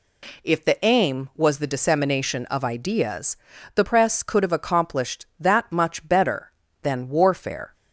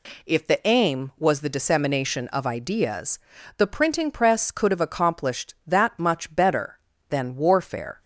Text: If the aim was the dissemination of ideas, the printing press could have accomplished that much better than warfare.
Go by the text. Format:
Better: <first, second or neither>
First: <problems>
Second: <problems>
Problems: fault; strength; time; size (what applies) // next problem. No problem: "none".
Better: second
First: skips "printing"; at 3.8 s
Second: none